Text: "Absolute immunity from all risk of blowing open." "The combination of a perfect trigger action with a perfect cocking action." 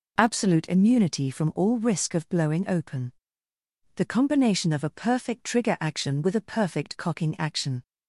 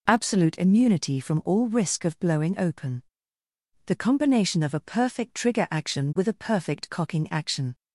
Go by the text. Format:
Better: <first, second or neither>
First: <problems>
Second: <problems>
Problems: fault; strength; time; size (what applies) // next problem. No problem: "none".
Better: neither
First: none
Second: none